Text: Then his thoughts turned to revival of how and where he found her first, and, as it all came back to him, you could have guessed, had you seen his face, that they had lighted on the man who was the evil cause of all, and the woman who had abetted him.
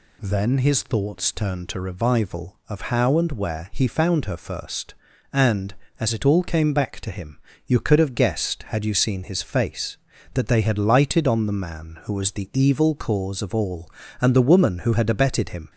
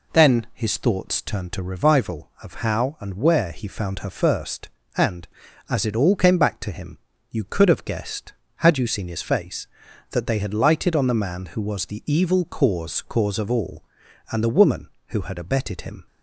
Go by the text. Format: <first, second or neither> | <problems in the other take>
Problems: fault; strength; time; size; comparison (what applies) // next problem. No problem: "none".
first | says "cause" twice; at 13.0 s